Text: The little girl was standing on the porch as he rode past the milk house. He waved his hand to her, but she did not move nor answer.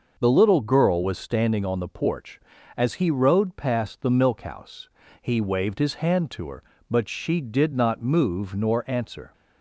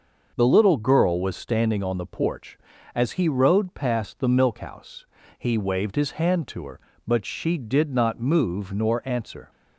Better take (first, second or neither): neither